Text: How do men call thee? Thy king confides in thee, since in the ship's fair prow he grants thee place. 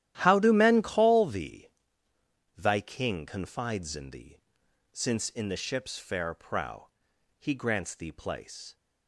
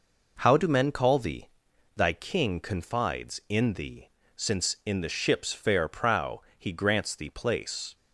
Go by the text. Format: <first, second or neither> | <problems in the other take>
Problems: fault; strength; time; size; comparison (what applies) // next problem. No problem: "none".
second | starts louder than the rest; strong; until 1.3 s; 12.5 dB // pauses between "prow" and "he"; noticeable; at 6.8 s; 0.50 s long; slight in the second